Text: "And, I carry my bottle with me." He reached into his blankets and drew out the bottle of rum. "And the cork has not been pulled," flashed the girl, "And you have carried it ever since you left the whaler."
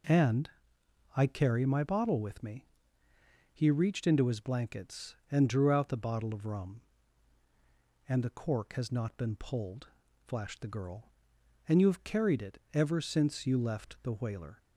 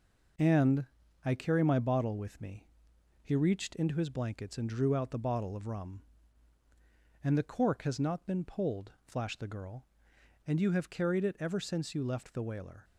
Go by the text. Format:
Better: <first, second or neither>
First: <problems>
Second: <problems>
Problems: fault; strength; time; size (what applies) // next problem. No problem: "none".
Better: neither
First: none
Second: none